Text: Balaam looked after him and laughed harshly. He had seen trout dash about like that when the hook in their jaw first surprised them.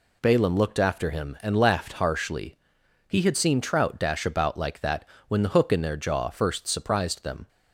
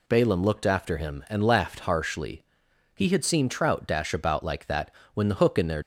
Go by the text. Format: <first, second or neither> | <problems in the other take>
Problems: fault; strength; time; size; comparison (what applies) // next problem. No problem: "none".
first | pauses between "that" and "when"; slight; at 4.9 s; 0.22 s long; slight in the first // stops before "jaw first surprised them"; at 5.8 s